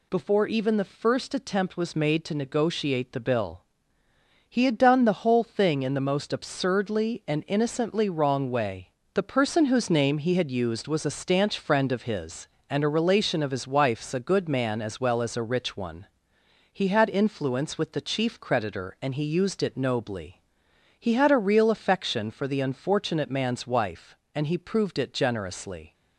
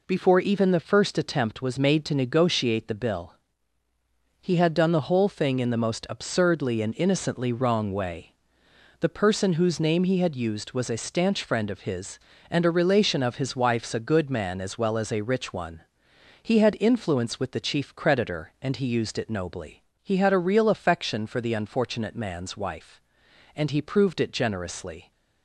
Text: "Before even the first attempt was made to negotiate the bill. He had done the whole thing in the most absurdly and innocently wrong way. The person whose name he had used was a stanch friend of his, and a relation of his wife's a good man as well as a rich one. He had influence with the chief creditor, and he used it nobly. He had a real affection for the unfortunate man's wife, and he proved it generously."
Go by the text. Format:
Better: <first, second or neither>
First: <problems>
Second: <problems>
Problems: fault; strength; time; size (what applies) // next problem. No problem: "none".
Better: neither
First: none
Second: none